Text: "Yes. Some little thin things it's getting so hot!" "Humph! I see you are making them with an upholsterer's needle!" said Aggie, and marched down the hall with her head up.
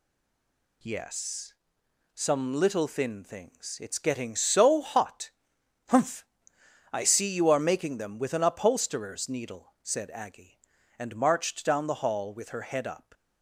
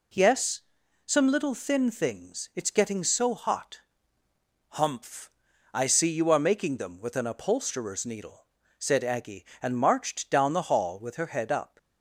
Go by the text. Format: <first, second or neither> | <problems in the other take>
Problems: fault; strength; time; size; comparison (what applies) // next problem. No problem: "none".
second | stays silent before the first word; slight; until 0.8 s; 0.8 s long